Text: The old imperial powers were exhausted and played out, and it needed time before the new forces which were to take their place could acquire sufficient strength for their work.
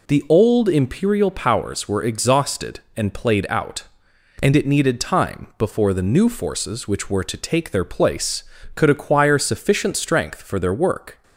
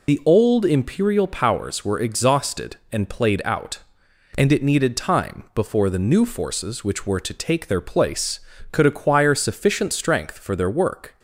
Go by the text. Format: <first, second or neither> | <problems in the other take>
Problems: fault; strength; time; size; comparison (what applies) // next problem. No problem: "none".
first | loses the start of "The"; at 0.0 s; 45 ms